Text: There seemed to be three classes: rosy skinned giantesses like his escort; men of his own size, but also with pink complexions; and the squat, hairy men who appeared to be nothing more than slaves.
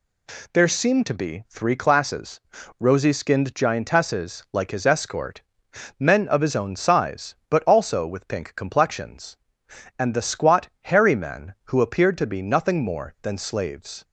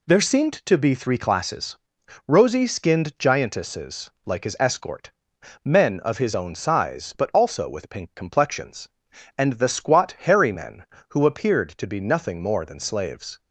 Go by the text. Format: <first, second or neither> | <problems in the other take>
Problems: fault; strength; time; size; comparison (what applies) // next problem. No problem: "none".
neither | none